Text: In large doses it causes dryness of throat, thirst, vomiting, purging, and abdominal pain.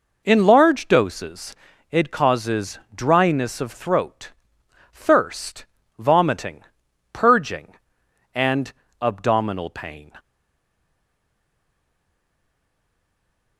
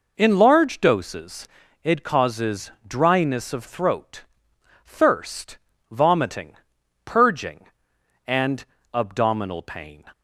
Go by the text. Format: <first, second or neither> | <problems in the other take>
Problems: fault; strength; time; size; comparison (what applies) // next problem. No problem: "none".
second | pauses between "doses" and "it"; at 1.5 s; 0.38 s long; also in the second // pauses between "causes" and "dryness"; slight; at 2.7 s; 0.16 s long; slight in the second // pauses between "and" and "abdominal"; slight; at 8.7 s; 0.30 s long; slight in the second // stays silent after the last word; strong; from 10.1 s on; 3.4 s long